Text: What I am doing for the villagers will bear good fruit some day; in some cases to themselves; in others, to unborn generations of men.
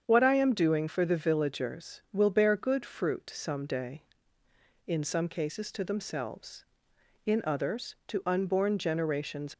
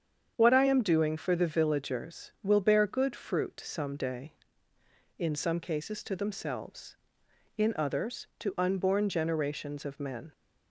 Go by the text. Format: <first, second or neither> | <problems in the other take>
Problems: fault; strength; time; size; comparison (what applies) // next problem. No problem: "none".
second | starts louder than the rest; strong; until 1.0 s; 7.5 dB; strong in the second // stops before "of men"; at 9.5 s